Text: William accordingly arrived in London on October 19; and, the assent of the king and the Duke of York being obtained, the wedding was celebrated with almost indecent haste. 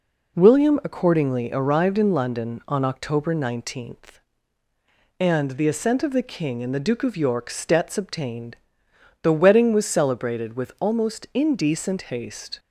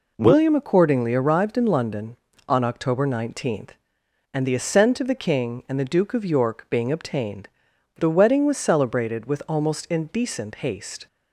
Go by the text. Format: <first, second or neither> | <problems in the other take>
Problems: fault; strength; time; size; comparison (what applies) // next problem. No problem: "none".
second | says "stets" for "being"; at 7.4 s